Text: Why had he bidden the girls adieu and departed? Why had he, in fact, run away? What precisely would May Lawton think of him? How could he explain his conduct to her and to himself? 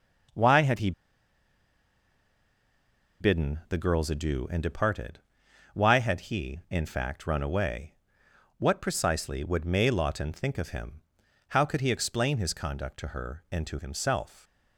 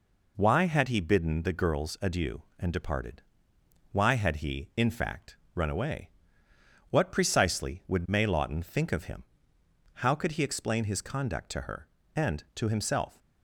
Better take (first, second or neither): second